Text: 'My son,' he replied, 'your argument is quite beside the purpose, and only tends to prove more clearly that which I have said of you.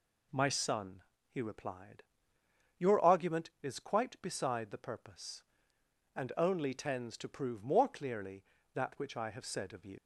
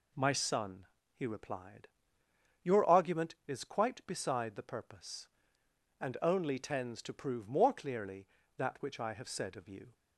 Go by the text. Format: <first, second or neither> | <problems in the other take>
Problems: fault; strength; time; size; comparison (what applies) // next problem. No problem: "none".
second | leaves "you" unfinished; at 9.9 s; 115 ms